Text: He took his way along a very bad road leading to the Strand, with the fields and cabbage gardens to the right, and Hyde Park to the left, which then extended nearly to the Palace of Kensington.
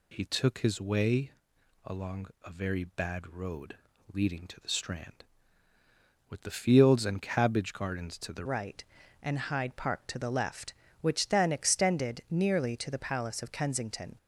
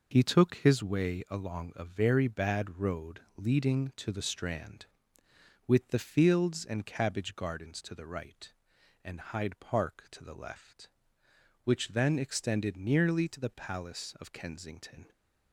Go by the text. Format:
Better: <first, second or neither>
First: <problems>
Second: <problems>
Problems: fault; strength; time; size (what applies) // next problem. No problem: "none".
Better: second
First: pauses between "way" and "along"; noticeable; at 1.3 s; 0.56 s long // pauses between "along" and "a"; slight; at 2.2 s; 0.18 s long // pauses between "road" and "leading"; slight; at 3.7 s; 0.36 s long // changes voice at "right"; from 8.4 s on; 5.7 s long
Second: pauses between "road" and "leading"; slight; at 3.2 s; 0.16 s long